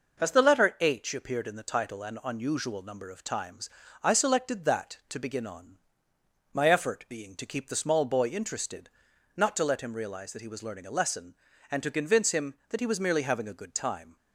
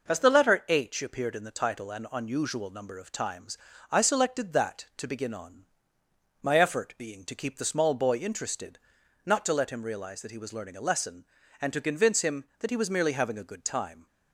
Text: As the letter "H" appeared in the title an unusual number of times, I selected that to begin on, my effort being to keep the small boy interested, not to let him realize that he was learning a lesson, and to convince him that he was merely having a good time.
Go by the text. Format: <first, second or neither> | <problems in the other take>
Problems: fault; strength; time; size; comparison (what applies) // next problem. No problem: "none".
neither | none